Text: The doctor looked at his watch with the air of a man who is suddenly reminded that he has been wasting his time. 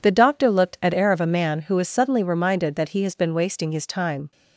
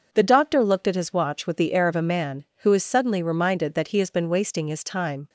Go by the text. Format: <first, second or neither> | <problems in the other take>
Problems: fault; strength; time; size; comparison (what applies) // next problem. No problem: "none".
second | skips "his watch with the"; at 0.9 s